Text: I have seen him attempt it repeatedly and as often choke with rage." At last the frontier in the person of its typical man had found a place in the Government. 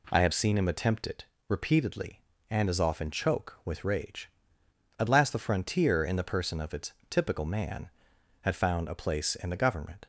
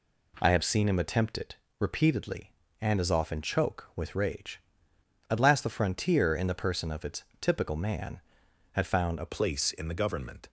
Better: first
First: pauses between "it" and "repeatedly"; slight; at 1.2 s; 0.24 s long // pauses between "its" and "typical"; slight; at 6.9 s; 0.18 s long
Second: pauses between "it" and "repeatedly"; slight; at 1.5 s; 0.24 s long // pauses between "its" and "typical"; slight; at 7.2 s; 0.18 s long // changes voice at "place"; from 9.2 s on; 1.2 s long

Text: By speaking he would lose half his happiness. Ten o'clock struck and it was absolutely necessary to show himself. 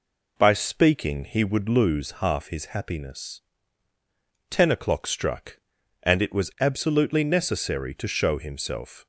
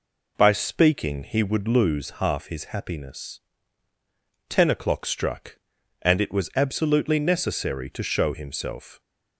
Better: neither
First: none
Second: none

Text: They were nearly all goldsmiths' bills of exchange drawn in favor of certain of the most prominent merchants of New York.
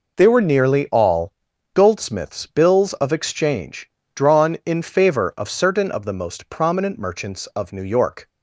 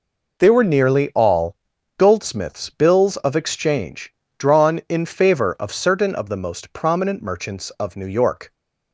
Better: neither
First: pauses between "all" and "goldsmiths"; at 1.3 s; 0.42 s long // pauses between "exchange" and "drawn"; slight; at 3.8 s; 0.24 s long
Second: pauses between "all" and "goldsmiths"; at 1.5 s; 0.42 s long // pauses between "exchange" and "drawn"; slight; at 4.1 s; 0.24 s long

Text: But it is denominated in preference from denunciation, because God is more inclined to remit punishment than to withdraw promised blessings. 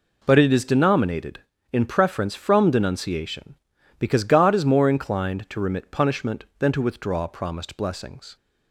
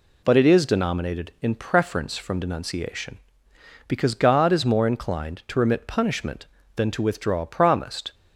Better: first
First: none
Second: stops before "blessings"; at 8.1 s

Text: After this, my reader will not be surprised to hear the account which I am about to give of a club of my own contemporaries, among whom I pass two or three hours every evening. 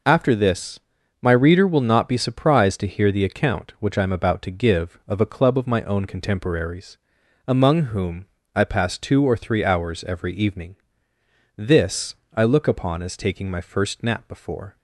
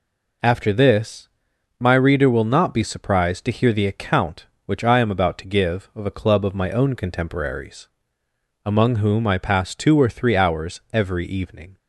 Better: second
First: pauses between "whom" and "I"; slight; at 8.2 s; 0.28 s long // goes on to say "This I look upon as taking my first nap before"; strong; from 11.5 s on; 3.2 s long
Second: none

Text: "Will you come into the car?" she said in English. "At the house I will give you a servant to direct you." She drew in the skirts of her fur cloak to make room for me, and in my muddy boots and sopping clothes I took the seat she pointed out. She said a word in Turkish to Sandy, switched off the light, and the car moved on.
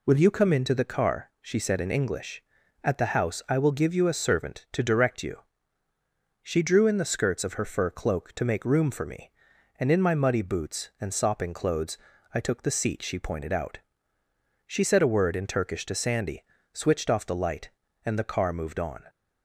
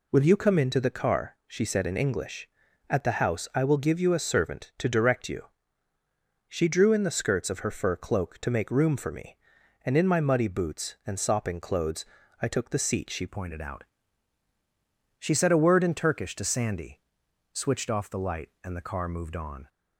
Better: first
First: pauses between "clothes" and "I"; slight; at 11.9 s; 0.36 s long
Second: pauses between "clothes" and "I"; slight; at 12.0 s; 0.36 s long // changes voice at "pointed"; from 13.2 s on; 6.4 s long

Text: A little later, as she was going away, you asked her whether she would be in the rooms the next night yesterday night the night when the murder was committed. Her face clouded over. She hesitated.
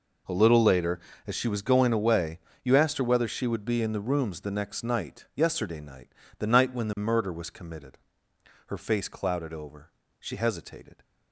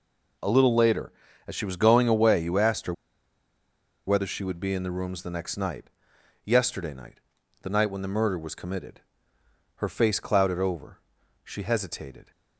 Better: first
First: pauses between "night" and "the"; slight; at 6.0 s; 0.32 s long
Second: pauses between "her" and "whether"; at 2.9 s; 1.1 s long // pauses between "night" and "yesterday"; noticeable; at 5.9 s; 0.52 s long // pauses between "night" and "the"; at 7.2 s; 0.40 s long

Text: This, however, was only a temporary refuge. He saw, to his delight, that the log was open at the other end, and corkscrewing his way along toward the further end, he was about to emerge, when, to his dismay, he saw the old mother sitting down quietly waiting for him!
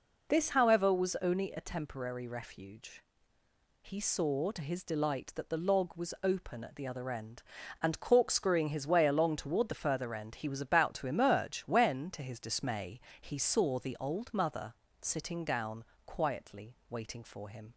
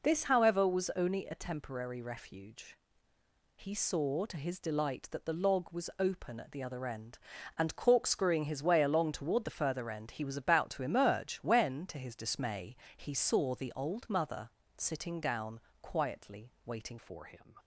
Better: first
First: pauses between "mother" and "sitting"; slight; at 14.7 s; 0.26 s long // pauses between "down" and "quietly"; slight; at 15.8 s; 0.22 s long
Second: pauses between "mother" and "sitting"; slight; at 14.4 s; 0.26 s long // pauses between "down" and "quietly"; slight; at 15.5 s; 0.22 s long // changes voice at "for"; from 16.9 s on; 0.6 s long

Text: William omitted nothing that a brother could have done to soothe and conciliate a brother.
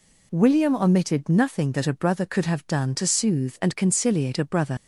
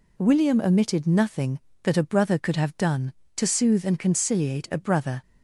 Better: second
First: leaves "brother" unfinished; at 4.7 s; 80 ms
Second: none

